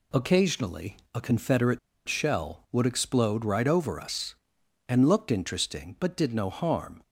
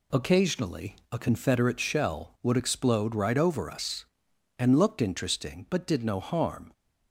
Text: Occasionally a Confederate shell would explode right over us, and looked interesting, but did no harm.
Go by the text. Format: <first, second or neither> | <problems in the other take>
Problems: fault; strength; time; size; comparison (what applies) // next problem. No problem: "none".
second | pauses between "Occasionally" and "a"; slight; at 0.9 s; 0.16 s long // pauses between "Confederate" and "shell"; slight; at 1.7 s; 0.27 s long